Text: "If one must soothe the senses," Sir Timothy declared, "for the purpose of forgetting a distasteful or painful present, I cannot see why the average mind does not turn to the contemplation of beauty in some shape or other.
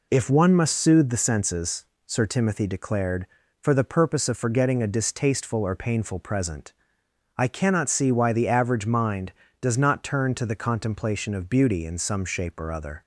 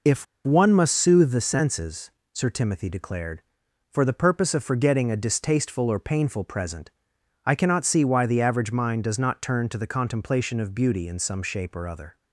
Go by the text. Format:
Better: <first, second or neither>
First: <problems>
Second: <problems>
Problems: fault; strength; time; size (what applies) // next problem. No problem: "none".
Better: first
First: none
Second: pauses between "If" and "one"; slight; at 0.2 s; 0.20 s long